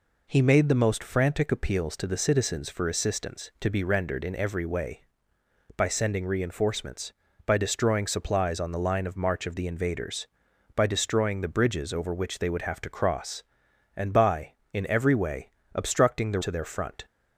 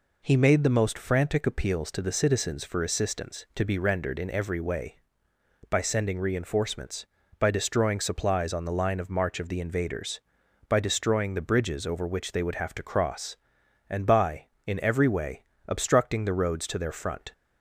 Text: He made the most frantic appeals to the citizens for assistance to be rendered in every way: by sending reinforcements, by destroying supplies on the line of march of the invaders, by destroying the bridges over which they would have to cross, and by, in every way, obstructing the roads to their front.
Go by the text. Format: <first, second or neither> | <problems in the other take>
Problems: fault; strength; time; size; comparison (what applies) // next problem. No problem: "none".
second | skips "roads"; at 16.4 s